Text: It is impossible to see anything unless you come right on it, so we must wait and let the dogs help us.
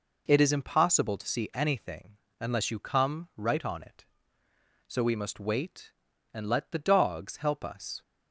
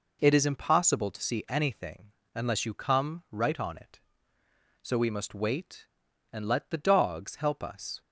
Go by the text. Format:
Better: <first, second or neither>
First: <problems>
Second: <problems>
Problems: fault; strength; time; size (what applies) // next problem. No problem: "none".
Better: neither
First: pauses between "anything" and "unless"; slight; at 2.1 s; 0.22 s long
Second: pauses between "anything" and "unless"; slight; at 2.1 s; 0.22 s long